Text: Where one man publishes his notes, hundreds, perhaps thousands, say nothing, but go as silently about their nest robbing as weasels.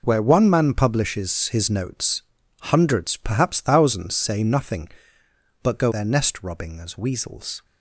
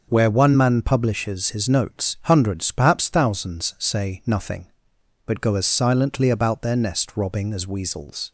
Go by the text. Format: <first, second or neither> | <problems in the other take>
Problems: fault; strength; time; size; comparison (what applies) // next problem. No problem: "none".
second | skips "as silently about"; at 5.9 s